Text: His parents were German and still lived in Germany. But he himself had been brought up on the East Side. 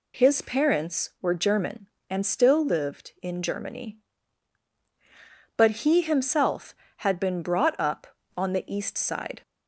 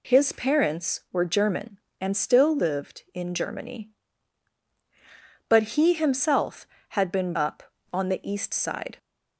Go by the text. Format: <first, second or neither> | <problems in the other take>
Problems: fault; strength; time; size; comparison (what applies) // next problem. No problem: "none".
first | skips "brought"; at 7.3 s